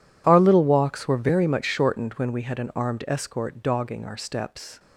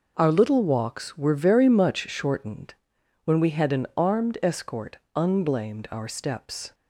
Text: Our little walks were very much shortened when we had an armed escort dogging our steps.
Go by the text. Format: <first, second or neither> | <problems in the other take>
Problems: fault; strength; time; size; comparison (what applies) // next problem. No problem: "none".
first | pauses between "shortened" and "when"; noticeable; at 2.7 s; 0.50 s long // says "unblamed" for "dogging"; at 5.1 s